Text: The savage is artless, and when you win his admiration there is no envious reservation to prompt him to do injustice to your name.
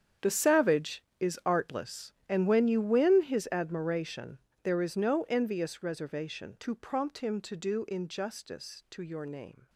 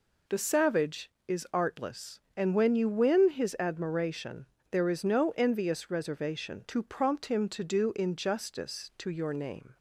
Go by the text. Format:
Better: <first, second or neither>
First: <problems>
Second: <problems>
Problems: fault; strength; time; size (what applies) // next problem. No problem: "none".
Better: second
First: gets quieter; strong; throughout; 16.5 dB // pauses between "admiration" and "there"; slight; at 4.3 s; 0.26 s long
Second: pauses between "admiration" and "there"; slight; at 4.4 s; 0.26 s long